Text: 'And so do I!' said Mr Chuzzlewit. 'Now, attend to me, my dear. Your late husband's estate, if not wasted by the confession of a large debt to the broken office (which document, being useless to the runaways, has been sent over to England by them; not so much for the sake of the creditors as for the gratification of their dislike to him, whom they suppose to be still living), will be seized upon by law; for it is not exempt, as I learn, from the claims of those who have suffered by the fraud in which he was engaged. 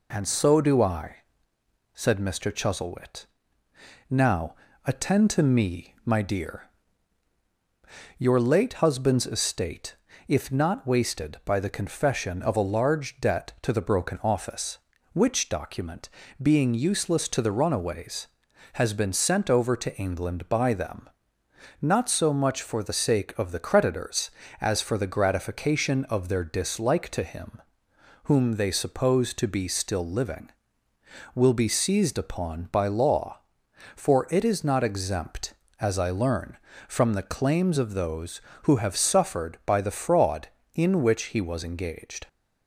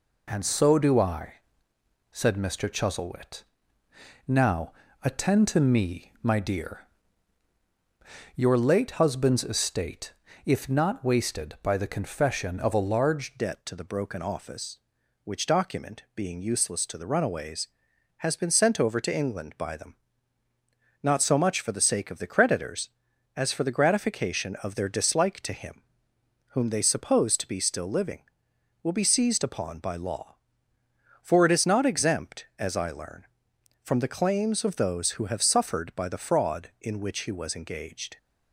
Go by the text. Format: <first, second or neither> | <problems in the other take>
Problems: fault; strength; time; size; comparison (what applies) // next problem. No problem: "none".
first | changes voice at "debt"; from 13.3 s on; 24.8 s long